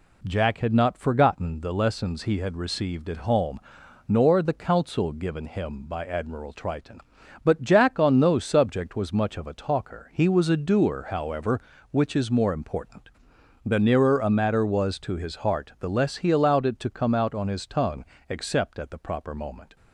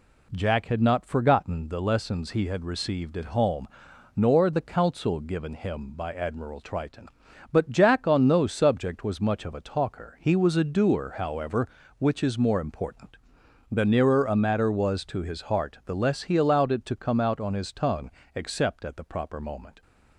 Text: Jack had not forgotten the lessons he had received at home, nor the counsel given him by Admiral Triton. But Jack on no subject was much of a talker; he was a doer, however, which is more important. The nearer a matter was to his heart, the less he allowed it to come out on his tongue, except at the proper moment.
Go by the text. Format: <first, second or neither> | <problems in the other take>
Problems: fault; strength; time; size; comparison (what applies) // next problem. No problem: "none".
neither | none